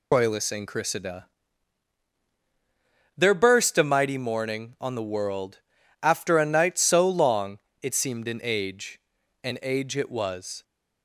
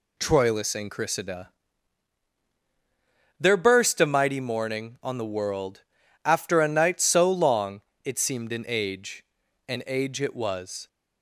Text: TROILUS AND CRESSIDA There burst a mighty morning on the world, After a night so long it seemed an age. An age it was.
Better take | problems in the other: second | loses the start of "TROILUS"; at 0.1 s; 170 ms // pauses between "CRESSIDA" and "There"; strong; at 1.2 s; 1.9 s long; strong in the second // pauses between "long" and "it"; slight; at 7.5 s; 0.22 s long; slight in the second

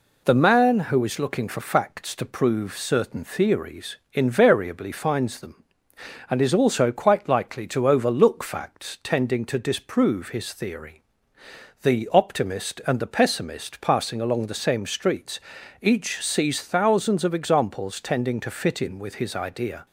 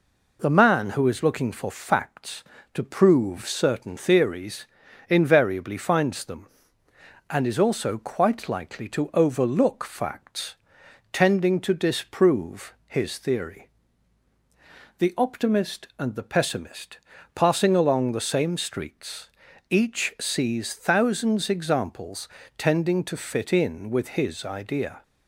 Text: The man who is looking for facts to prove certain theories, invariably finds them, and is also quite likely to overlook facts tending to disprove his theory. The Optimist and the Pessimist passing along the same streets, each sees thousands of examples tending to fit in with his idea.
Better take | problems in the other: first | pauses between "facts" and "tending"; noticeable; at 10.5 s; 0.58 s long // pauses between "disprove" and "his"; slight; at 12.7 s; 0.16 s long // pauses between "Pessimist" and "passing"; at 16.9 s; 0.38 s long // skips "of"; at 21.5 s // pauses between "examples" and "tending"; slight; at 22.2 s; 0.28 s long

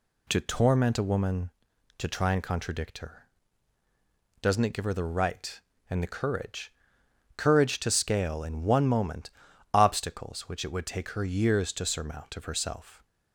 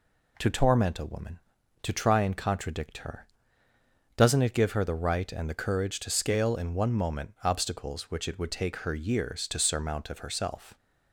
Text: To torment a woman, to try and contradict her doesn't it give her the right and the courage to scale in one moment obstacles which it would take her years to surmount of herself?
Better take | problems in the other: second | pauses between "her" and "doesn't"; at 3.2 s; 1.2 s long; noticeable in the second // says "courage" twice; at 7.3 s // pauses between "moment" and "obstacles"; at 9.2 s; 0.42 s long

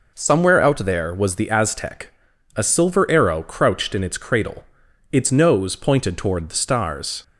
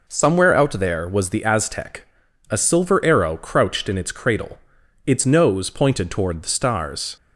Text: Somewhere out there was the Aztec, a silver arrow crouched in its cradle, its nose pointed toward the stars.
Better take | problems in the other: neither | none

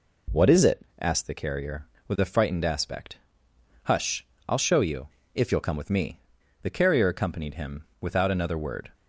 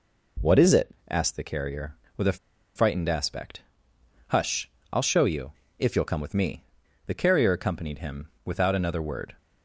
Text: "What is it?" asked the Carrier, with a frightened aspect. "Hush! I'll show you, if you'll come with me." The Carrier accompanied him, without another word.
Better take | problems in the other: first | pauses between "a" and "frightened"; at 2.3 s; 0.37 s long

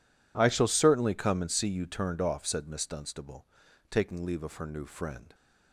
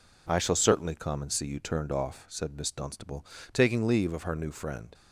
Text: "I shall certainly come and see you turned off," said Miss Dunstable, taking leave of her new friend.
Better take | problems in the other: neither | none

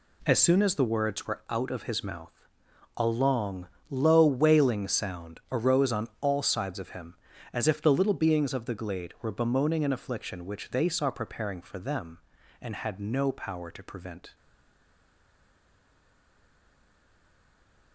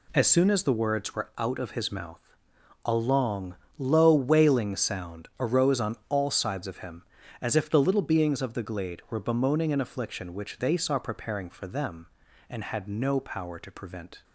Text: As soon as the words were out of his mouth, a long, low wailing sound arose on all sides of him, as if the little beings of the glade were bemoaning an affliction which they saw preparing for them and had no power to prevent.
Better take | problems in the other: second | stays silent after the last word; strong; from 14.3 s on; 3.6 s long

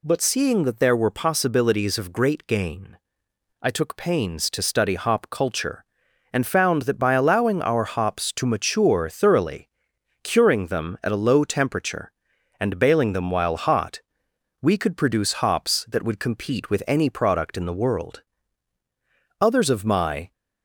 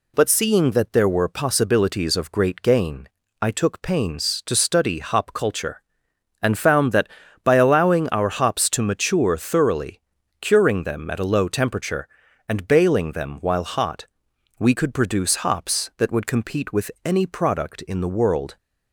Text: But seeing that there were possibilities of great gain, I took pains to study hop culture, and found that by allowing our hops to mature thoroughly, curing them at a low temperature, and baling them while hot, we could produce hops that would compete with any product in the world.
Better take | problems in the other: second | goes on to say "Others of my"; noticeable; from 19.3 s on; 0.92 s long

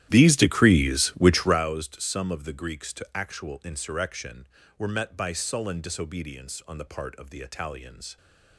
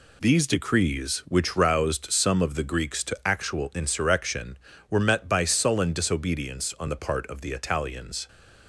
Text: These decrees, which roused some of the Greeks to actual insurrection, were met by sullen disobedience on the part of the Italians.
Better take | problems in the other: second | starts louder than the rest; strong; until 1.7 s; 12.5 dB

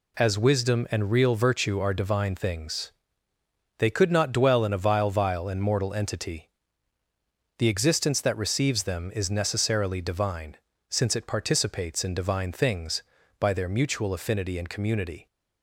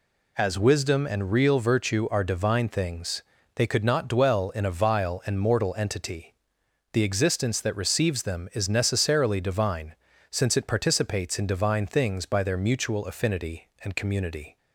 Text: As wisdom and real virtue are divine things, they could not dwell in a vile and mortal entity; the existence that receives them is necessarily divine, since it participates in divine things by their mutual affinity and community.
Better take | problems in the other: second | says "vile" twice; at 5.1 s

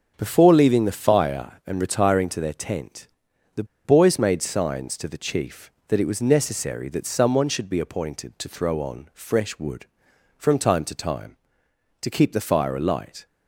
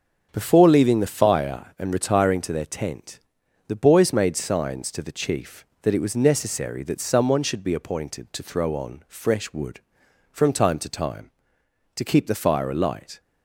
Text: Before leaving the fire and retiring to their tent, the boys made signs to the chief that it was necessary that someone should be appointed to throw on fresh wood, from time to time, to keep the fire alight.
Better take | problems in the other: second | starts louder than the rest; until 1.1 s; 6.5 dB; also in the second // pauses between "the" and "boys"; slight; at 3.6 s; 0.20 s long

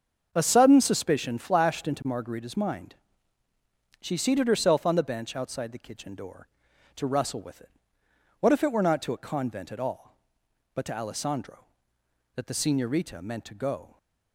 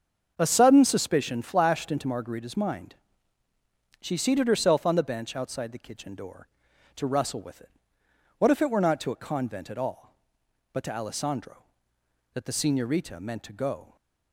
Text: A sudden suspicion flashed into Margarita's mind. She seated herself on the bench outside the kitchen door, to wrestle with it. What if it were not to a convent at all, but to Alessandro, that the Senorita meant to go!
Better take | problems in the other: neither | starts louder than the rest; the same in both

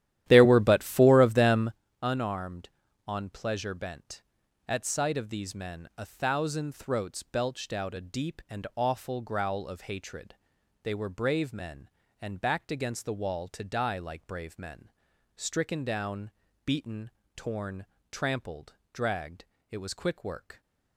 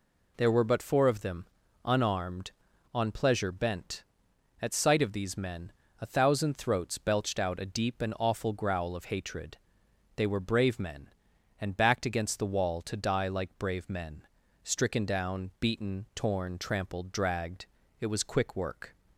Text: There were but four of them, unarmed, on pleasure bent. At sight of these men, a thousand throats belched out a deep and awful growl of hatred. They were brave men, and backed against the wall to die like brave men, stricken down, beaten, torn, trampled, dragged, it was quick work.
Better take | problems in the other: second | starts louder than the rest; strong; until 1.8 s; 12.5 dB

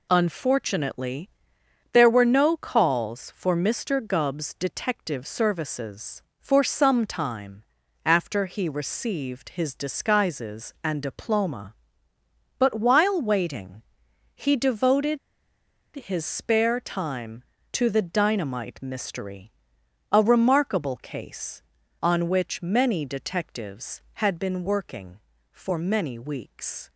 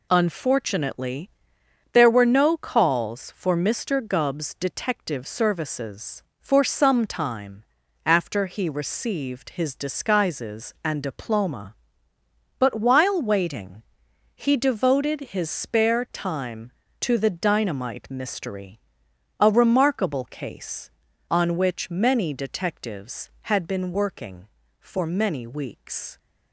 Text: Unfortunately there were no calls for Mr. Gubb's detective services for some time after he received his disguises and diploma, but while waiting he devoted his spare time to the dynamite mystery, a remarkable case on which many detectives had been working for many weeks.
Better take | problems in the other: second | pauses between "Unfortunately" and "there"; noticeable; at 1.2 s; 0.62 s long; noticeable in the second // pauses between "time" and "after"; at 7.6 s; 0.40 s long; also in the second // pauses between "waiting" and "he"; noticeable; at 13.8 s; 0.54 s long; noticeable in the second // pauses between "devoted" and "his"; noticeable; at 15.1 s; 0.77 s long

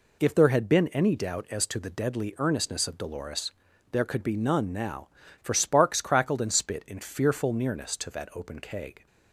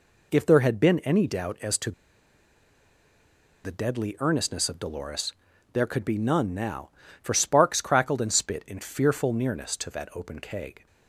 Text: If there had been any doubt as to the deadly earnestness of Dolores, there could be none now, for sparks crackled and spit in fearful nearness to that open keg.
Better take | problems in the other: first | pauses between "to" and "the"; strong; at 1.9 s; 1.7 s long

